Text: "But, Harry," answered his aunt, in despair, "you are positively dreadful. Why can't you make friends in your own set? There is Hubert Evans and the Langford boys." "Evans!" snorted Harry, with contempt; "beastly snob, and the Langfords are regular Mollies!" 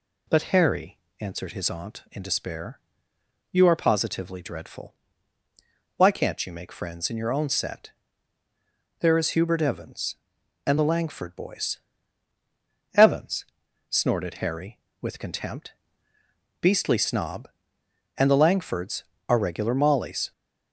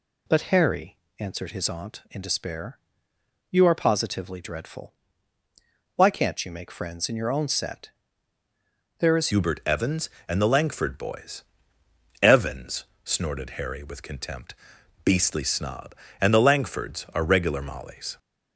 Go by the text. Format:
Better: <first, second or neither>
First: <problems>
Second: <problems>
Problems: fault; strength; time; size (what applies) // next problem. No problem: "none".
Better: first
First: none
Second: changes voice at "Hubert"; from 9.3 s on; 8.8 s long